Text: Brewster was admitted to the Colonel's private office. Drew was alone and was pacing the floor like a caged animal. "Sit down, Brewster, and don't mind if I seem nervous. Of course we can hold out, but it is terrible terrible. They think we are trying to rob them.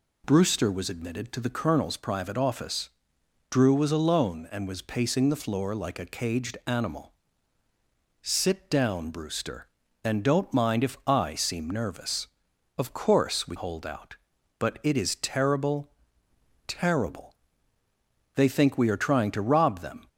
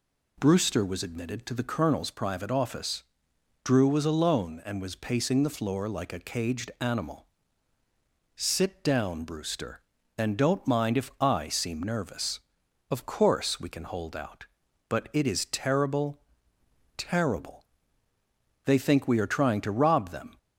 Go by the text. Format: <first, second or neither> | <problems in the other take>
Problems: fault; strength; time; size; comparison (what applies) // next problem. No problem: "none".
second | skips "can"; at 13.5 s // pauses between "terrible" and "terrible"; noticeable; at 15.8 s; 0.78 s long; noticeable in the second